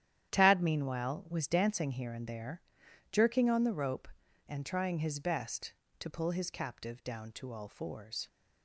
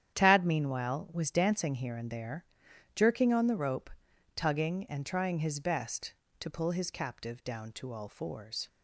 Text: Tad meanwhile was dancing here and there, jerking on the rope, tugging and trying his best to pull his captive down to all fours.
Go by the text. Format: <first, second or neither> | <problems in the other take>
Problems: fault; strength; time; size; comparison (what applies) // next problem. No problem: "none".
second | starts louder than the rest; strong; until 1.3 s; 10.5 dB; strong in the second // skips "tugging"; at 4.2 s